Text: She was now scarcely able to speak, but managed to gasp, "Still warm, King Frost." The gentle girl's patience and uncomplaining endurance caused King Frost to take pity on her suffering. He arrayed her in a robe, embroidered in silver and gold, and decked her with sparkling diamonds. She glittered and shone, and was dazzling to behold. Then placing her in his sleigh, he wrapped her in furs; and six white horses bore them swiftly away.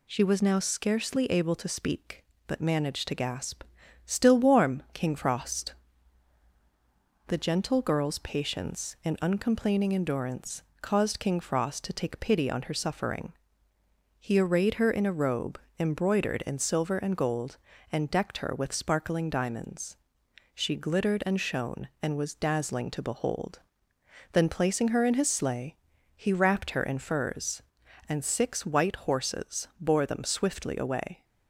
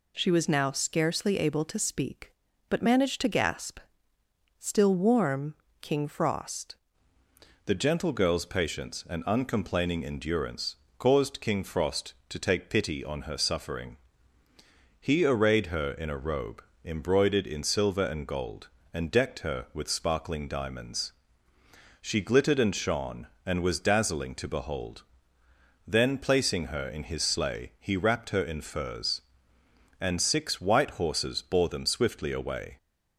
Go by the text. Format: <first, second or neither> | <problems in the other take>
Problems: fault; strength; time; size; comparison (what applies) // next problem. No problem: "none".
first | changes voice at "The"; from 7.6 s on; 25.1 s long // pauses between "endurance" and "caused"; slight; at 10.7 s; 0.24 s long; slight in the first